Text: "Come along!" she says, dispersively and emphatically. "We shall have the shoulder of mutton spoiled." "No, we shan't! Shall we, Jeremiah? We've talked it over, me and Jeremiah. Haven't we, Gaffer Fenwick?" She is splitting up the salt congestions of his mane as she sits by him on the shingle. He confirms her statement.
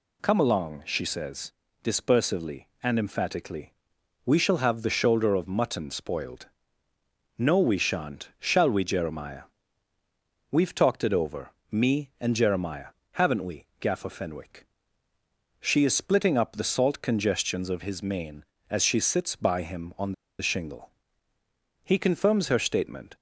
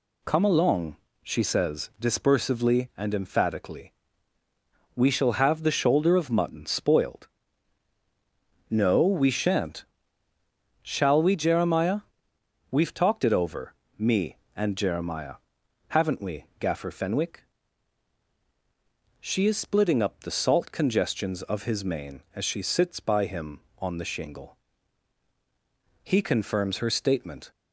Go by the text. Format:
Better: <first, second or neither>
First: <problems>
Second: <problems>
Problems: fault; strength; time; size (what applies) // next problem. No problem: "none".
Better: second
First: pauses between "on" and "the"; slight; at 20.1 s; 0.26 s long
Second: none